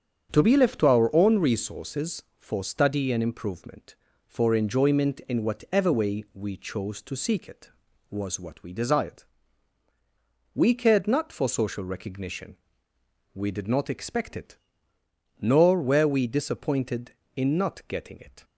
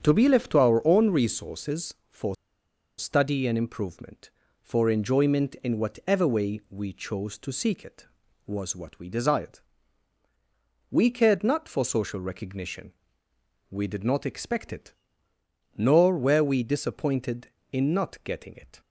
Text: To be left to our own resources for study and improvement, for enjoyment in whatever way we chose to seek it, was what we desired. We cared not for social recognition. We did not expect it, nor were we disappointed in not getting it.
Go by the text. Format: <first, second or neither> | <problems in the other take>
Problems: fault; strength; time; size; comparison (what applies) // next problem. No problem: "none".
first | starts louder than the rest; strong; until 1.0 s; 7.5 dB; strong in the first // pauses between "for" and "study"; noticeable; at 2.3 s; 0.63 s long